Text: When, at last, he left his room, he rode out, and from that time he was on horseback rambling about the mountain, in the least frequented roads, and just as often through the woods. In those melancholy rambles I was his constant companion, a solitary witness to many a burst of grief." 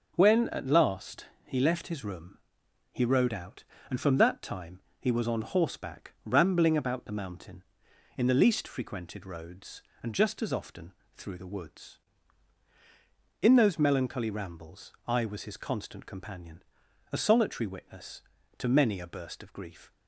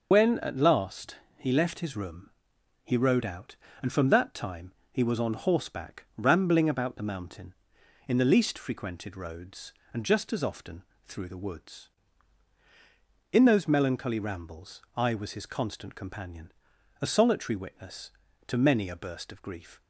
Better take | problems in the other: first | loses the start of "When"; at 0.1 s; 55 ms // pauses between "time" and "he"; slight; at 4.7 s; 0.20 s long; slight in the first // pauses between "often" and "through"; slight; at 10.8 s; 0.22 s long; slight in the first // pauses between "rambles" and "I"; slight; at 14.8 s; 0.16 s long; slight in the first

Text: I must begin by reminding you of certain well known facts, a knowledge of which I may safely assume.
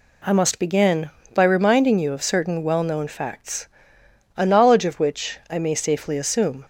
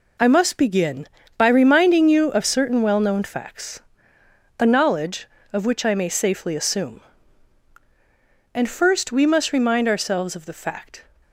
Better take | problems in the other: first | goes on to say "And first we must remind ourselves of the fact"; strong; from 8.5 s on; 2.5 s long

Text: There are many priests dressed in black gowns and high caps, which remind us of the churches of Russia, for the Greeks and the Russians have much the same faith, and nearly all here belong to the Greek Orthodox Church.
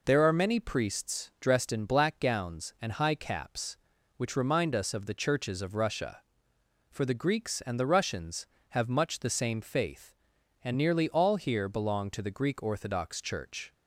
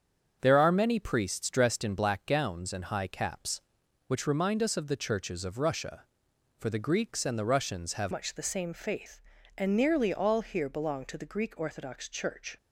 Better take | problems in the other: first | starts louder than the rest; strong; until 1.4 s; 7.5 dB // changes voice at "much"; from 8.1 s on; 4.4 s long

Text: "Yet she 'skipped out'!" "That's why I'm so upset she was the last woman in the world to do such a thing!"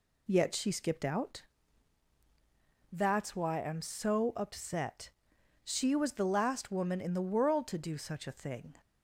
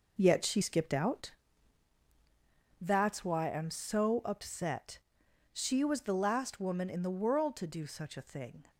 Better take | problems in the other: first | gets quieter; strong; throughout; 8.5 dB // pauses between "upset" and "she"; noticeable; at 4.9 s; 0.52 s long; noticeable in the first

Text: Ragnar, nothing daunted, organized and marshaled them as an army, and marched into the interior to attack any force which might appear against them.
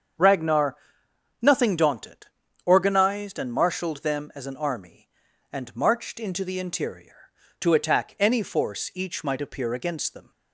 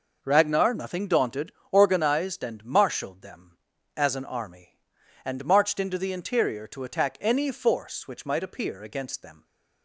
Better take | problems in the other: second | starts louder than the rest; strong; until 1.8 s; 7.5 dB // says "each" for "which"; at 8.9 s

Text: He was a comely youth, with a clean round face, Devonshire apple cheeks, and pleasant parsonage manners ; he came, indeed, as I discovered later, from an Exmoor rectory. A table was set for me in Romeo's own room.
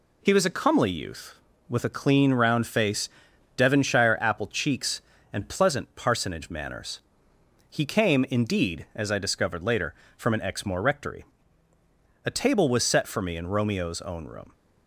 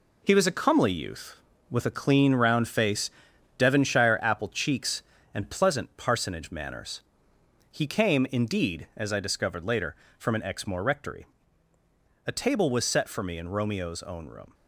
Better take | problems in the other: first | gets quieter; strong; throughout; 8 dB

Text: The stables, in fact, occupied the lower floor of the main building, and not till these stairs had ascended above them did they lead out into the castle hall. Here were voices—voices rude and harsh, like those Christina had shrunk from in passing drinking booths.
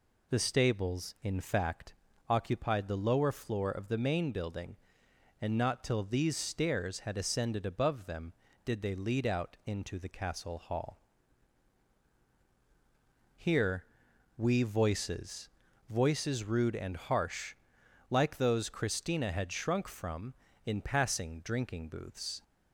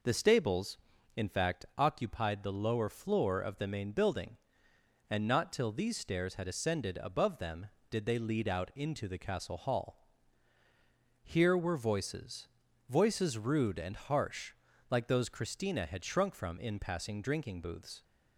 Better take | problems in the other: second | says "we" for "were"; at 14.3 s

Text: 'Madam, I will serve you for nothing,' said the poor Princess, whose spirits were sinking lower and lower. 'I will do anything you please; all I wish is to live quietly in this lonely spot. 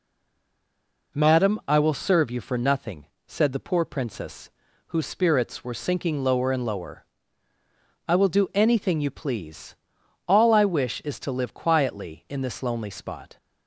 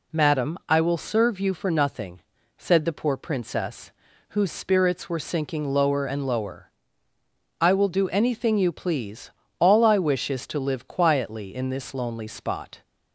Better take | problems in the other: second | stays silent before the first word; until 1.1 s; 1.1 s long

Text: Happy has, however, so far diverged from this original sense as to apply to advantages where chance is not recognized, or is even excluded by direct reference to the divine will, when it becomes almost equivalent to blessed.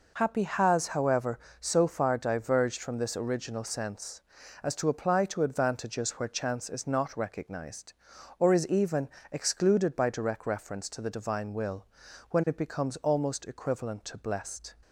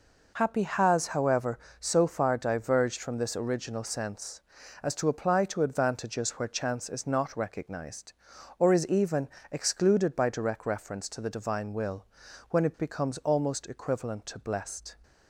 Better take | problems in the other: neither | pauses between "even" and "excluded"; slight; the same in both

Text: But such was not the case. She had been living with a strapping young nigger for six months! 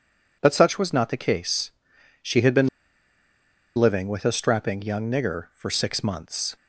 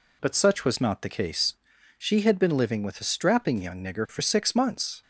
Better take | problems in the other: second | pauses between "been" and "living"; at 2.6 s; 1.0 s long

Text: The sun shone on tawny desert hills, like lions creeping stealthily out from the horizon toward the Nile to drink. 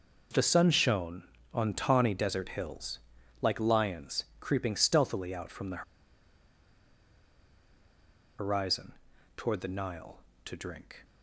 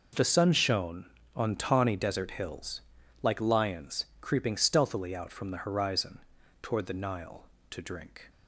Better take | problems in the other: second | pauses between "lions" and "creeping"; slight; at 4.2 s; 0.16 s long; slight in the second // pauses between "the" and "horizon"; strong; at 5.8 s; 2.5 s long // pauses between "horizon" and "toward"; at 8.9 s; 0.44 s long; also in the second

